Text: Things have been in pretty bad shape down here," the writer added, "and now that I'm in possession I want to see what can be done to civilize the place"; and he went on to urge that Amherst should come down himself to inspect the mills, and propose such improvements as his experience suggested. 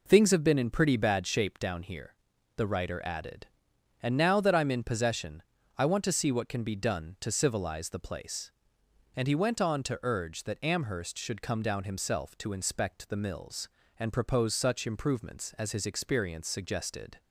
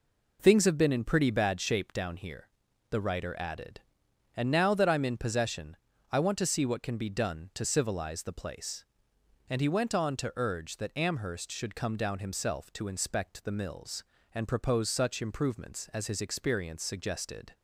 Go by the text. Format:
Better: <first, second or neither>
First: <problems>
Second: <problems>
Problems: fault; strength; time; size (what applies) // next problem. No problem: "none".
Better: neither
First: pauses between "possession" and "I"; slight; at 5.4 s; 0.34 s long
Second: pauses between "possession" and "I"; slight; at 5.7 s; 0.34 s long